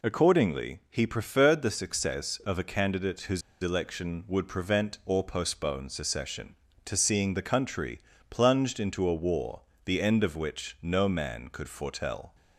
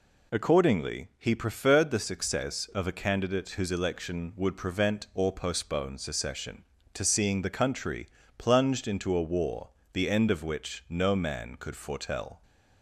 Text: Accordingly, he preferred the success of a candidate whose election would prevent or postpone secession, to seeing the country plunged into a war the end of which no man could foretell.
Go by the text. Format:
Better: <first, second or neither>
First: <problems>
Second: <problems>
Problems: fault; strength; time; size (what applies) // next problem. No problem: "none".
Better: second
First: pauses between "whose" and "election"; slight; at 3.4 s; 0.21 s long // pauses between "country" and "plunged"; slight; at 8.0 s; 0.28 s long // pauses between "war" and "the"; slight; at 9.6 s; 0.24 s long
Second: pauses between "country" and "plunged"; slight; at 8.0 s; 0.28 s long // pauses between "war" and "the"; slight; at 9.6 s; 0.24 s long